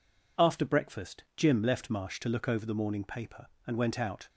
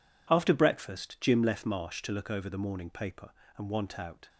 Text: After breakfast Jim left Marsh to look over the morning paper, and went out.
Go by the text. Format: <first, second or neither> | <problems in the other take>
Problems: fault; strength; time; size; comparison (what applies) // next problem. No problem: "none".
first | says "want" for "went"; at 3.7 s